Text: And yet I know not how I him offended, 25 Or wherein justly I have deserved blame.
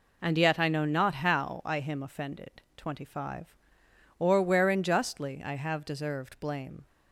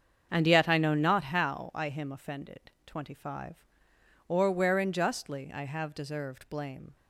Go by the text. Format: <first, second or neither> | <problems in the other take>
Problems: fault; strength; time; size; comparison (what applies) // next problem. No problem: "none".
first | starts louder than the rest; strong; until 1.3 s; 7.5 dB